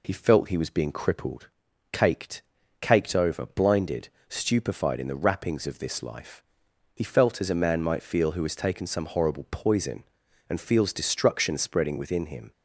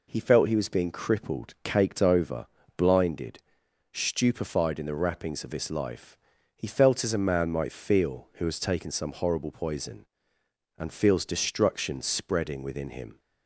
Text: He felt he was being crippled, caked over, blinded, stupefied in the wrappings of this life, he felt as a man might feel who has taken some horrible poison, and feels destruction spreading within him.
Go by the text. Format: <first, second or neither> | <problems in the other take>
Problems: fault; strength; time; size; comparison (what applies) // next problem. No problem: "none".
second | says "caked" twice; at 2.7 s